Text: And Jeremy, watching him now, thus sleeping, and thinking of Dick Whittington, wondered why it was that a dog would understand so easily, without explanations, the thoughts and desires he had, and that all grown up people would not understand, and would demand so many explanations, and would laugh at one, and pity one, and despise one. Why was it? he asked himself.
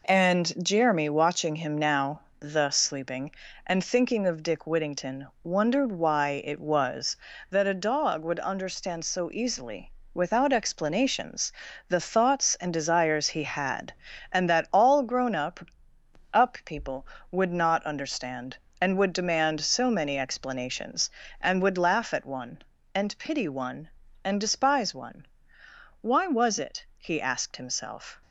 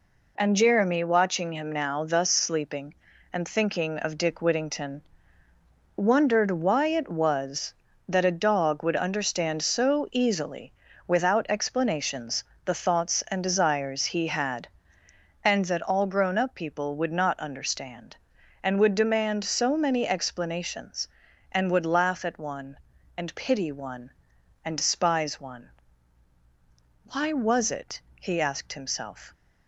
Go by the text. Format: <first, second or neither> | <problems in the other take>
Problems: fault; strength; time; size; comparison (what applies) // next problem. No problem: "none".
second | says "up" twice; at 16.3 s